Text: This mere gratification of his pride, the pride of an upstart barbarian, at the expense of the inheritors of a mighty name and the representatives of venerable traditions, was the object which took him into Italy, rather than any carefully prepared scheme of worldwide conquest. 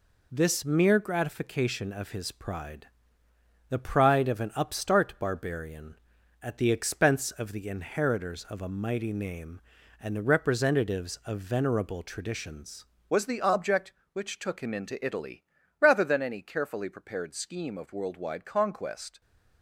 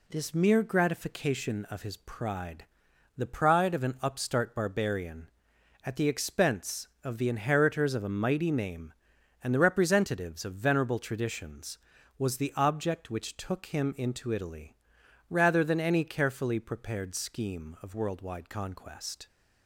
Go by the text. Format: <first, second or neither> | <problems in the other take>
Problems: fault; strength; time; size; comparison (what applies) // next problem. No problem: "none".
second | changes voice at "was"; from 13.0 s on; 6.2 s long